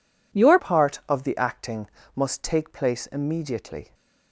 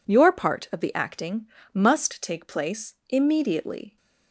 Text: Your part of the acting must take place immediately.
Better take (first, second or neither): second